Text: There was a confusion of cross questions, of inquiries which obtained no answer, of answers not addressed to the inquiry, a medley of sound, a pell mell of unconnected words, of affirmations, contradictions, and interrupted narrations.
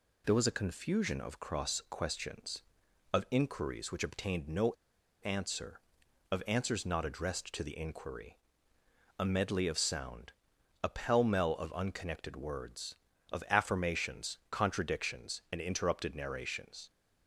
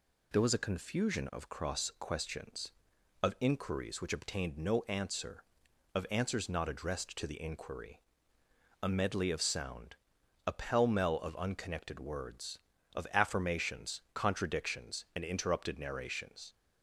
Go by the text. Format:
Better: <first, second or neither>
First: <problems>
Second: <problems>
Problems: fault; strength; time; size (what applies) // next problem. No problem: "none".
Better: second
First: pauses between "no" and "answer"; noticeable; at 4.7 s; 0.52 s long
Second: none